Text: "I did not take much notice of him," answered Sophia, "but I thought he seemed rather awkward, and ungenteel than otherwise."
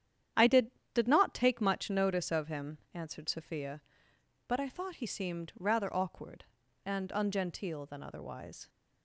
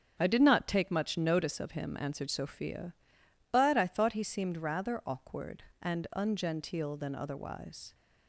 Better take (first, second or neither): second